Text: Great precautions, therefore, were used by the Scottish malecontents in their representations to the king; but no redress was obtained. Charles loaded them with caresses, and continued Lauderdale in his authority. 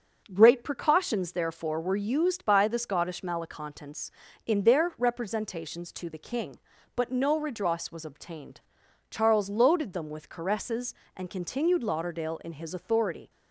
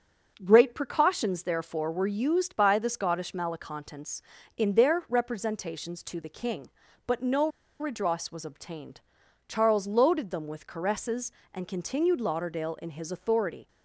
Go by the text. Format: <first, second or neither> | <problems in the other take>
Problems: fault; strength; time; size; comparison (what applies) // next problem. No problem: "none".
first | starts louder than the rest; until 1.4 s; 6.5 dB; also in the first // pauses between "no" and "redress"; slight; at 7.4 s; 0.31 s long